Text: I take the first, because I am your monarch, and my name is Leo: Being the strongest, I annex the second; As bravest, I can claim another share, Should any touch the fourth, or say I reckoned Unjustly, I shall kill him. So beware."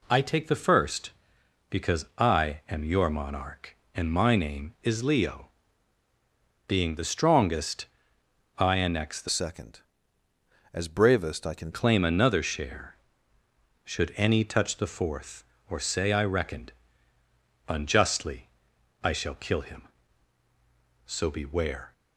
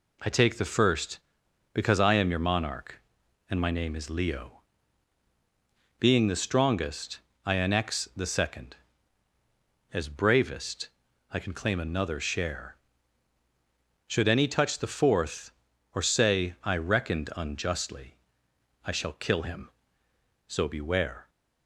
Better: second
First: changes voice from "second" to "can"; from 9.2 to 11.7 s; 2.5 s long // pauses between "reckoned" and "Unjustly"; noticeable; at 16.7 s; 0.96 s long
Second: none

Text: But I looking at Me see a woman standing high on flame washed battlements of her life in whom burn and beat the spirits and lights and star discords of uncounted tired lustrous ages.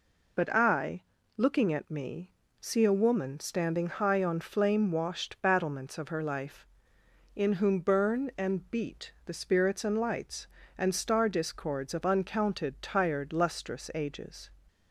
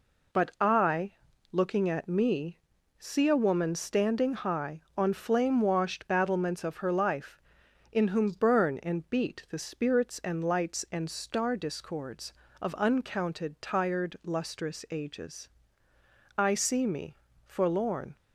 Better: first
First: pauses between "I" and "looking"; slight; at 1.0 s; 0.34 s long // pauses between "Me" and "see"; slight; at 2.2 s; 0.30 s long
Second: pauses between "I" and "looking"; slight; at 1.1 s; 0.36 s long // pauses between "Me" and "see"; slight; at 2.6 s; 0.36 s long // goes on to say "I see me forlorn"; strong; from 16.3 s on; 1.7 s long

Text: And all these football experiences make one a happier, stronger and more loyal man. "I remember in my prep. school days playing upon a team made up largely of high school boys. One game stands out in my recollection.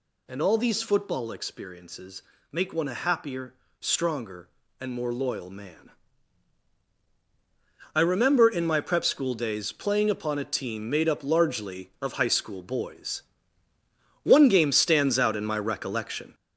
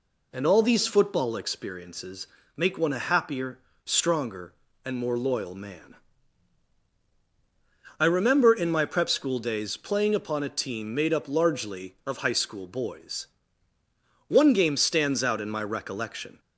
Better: second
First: gets louder; noticeable; throughout; 6 dB // pauses between "experiences" and "make"; slight; at 2.2 s; 0.28 s long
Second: pauses between "experiences" and "make"; slight; at 2.2 s; 0.28 s long

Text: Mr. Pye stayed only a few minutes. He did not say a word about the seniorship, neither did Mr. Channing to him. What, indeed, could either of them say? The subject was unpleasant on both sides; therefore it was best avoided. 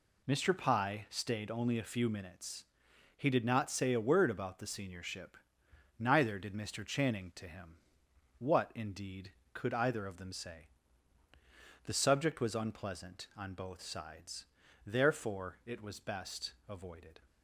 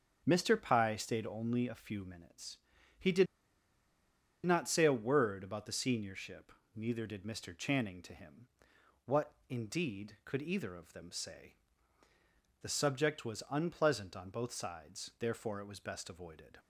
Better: first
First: none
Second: starts louder than the rest; until 1.2 s; 7 dB // pauses between "did" and "not"; at 3.2 s; 1.2 s long

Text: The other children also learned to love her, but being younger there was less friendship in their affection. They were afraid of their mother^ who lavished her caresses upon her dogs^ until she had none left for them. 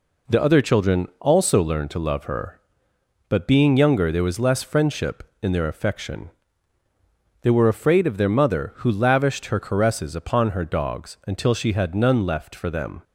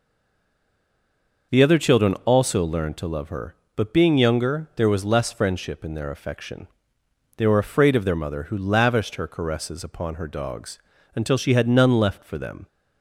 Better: first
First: none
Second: stays silent before the first word; noticeable; until 1.5 s; 1.5 s long // pauses between "dogs" and "until"; at 10.7 s; 0.38 s long

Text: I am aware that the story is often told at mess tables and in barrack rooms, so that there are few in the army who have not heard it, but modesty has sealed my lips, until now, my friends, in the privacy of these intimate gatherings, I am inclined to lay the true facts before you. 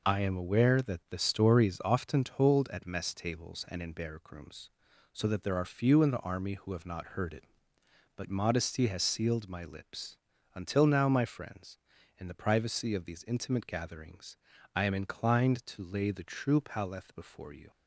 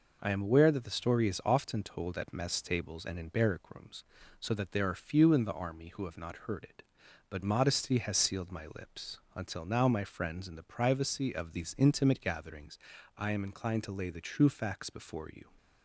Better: second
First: says "paleth" for "facts"; at 16.6 s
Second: none

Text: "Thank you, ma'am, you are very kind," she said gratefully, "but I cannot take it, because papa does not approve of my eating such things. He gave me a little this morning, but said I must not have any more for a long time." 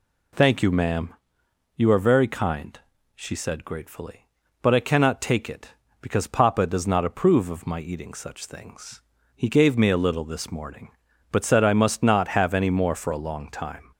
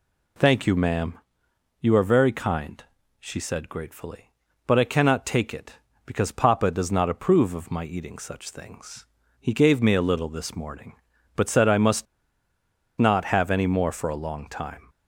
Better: first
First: none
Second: pauses between "must" and "not"; noticeable; at 12.0 s; 0.93 s long

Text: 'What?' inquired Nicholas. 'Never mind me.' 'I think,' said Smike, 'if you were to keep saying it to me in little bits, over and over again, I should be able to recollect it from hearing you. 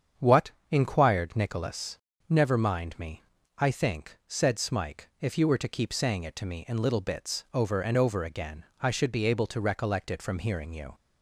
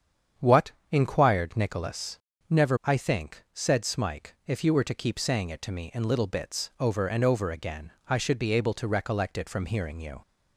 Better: first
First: starts louder than the rest; strong; until 1.3 s; 7.5 dB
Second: starts louder than the rest; strong; until 1.5 s; 8 dB // skips "mind me"; at 2.7 s

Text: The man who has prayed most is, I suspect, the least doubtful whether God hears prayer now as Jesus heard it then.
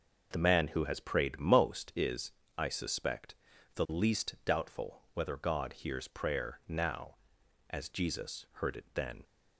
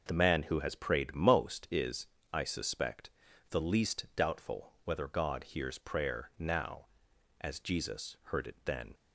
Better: neither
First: none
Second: none

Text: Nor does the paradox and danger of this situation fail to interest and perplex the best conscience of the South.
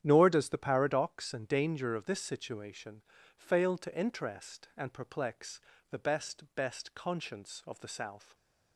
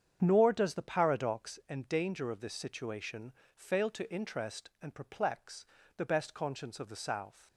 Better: second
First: starts louder than the rest; strong; until 1.0 s; 10 dB // pauses between "situation" and "fail"; slight; at 3.0 s; 0.34 s long // pauses between "perplex" and "the"; slight; at 5.6 s; 0.30 s long // says "best" twice; at 6.5 s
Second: starts louder than the rest; strong; until 1.2 s; 8 dB // pauses between "situation" and "fail"; slight; at 3.3 s; 0.24 s long // pauses between "perplex" and "the"; slight; at 5.6 s; 0.32 s long

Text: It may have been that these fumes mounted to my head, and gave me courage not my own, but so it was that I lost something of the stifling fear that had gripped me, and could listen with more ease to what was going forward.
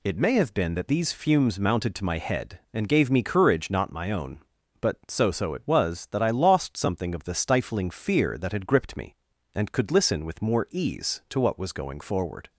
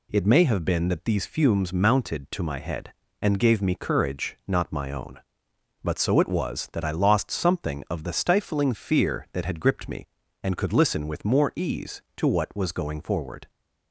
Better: second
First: says "so" twice; at 5.3 s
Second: none

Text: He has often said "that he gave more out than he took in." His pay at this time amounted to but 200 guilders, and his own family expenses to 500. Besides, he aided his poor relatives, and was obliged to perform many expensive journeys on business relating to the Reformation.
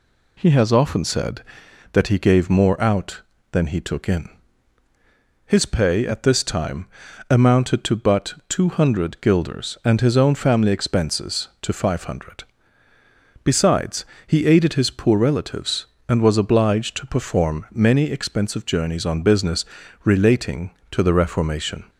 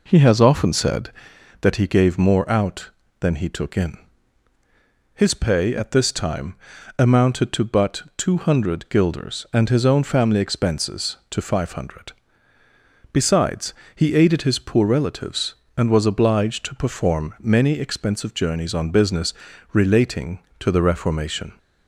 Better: first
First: pauses between "time" and "amounted"; at 6.8 s; 0.42 s long // pauses between "business" and "relating"; at 19.6 s; 0.40 s long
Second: starts louder than the rest; noticeable; until 1.1 s; 4 dB // pauses between "time" and "amounted"; at 6.5 s; 0.42 s long // pauses between "business" and "relating"; at 19.3 s; 0.40 s long

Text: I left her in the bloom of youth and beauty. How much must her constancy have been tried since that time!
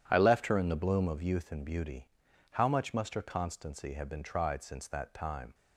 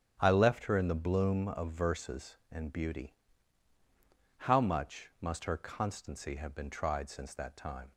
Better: first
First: starts louder than the rest; strong; until 1.0 s; 10 dB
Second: starts louder than the rest; strong; until 1.2 s; 9 dB // says "verses" for "youth"; at 1.7 s

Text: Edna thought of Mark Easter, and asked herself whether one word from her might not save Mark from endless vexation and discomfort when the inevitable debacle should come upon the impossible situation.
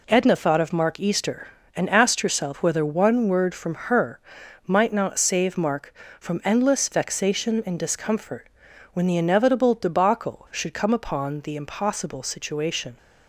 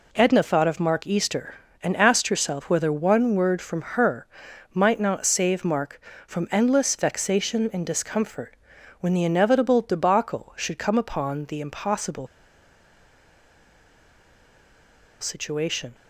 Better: first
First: pauses between "her" and "might"; noticeable; at 4.2 s; 0.46 s long // pauses between "discomfort" and "when"; at 8.5 s; 0.42 s long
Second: pauses between "her" and "might"; noticeable; at 4.2 s; 0.46 s long // pauses between "discomfort" and "when"; at 8.5 s; 0.42 s long // pauses between "impossible" and "situation"; strong; at 12.2 s; 2.9 s long

